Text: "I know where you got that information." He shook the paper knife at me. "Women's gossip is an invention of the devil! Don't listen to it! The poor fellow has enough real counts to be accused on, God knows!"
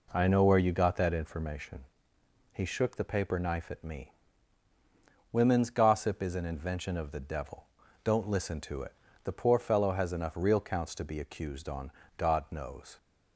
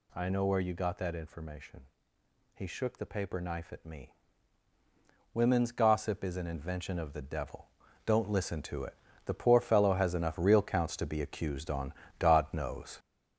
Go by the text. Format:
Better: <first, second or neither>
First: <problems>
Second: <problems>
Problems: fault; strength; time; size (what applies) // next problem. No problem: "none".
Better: first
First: none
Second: gets louder; throughout; 7 dB